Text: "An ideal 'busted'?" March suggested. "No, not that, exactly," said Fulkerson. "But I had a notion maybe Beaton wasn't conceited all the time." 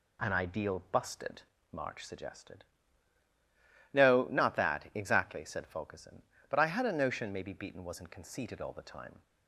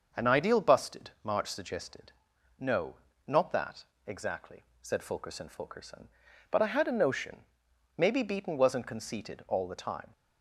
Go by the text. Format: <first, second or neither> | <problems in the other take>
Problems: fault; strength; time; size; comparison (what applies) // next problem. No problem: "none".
first | starts louder than the rest; until 1.2 s; 6.5 dB // says "Fulkerson" twice; at 5.4 s // pauses between "notion" and "maybe"; noticeable; at 7.4 s; 0.50 s long